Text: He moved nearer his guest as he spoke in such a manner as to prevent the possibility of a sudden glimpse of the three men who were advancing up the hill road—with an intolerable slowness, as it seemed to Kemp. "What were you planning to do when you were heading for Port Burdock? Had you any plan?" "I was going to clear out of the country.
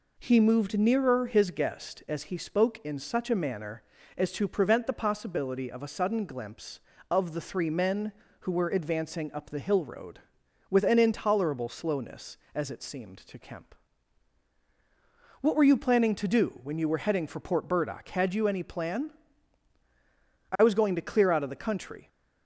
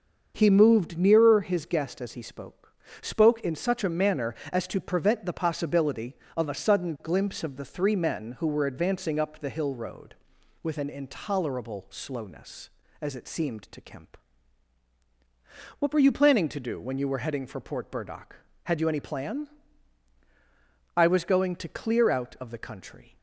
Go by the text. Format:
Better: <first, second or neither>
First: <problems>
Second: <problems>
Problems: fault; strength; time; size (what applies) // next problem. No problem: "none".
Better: first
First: none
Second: starts louder than the rest; until 1.3 s; 6.5 dB // says "spoke" twice; at 3.0 s